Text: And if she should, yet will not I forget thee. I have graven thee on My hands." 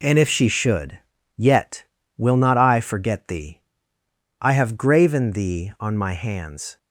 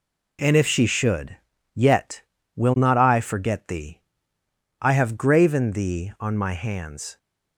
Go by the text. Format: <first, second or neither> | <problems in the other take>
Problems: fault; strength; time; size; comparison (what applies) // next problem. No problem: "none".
neither | none